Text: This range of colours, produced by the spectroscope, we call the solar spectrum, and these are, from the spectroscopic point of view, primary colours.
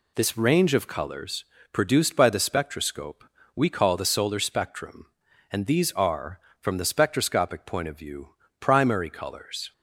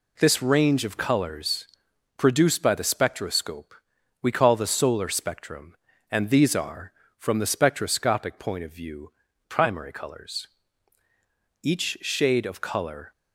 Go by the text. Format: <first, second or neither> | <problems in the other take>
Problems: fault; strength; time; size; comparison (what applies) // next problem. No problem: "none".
first | goes on to say "Each shade of colour"; from 11.6 s on; 1.4 s long